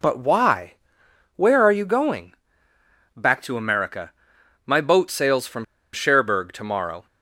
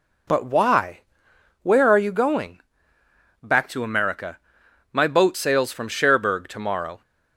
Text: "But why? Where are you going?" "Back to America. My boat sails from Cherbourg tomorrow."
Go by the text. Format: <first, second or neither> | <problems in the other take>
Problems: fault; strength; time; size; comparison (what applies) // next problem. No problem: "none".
second | pauses between "from" and "Cherbourg"; slight; at 5.6 s; 0.29 s long